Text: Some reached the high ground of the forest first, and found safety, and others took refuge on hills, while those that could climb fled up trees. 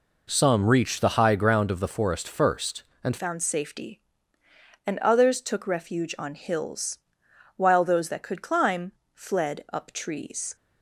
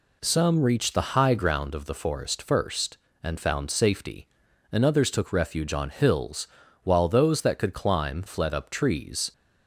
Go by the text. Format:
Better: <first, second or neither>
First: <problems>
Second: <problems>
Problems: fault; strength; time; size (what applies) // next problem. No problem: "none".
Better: second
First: changes voice at "found"; from 3.1 s on; 7.4 s long // pauses between "climb" and "fled"; slight; at 8.9 s; 0.20 s long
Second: none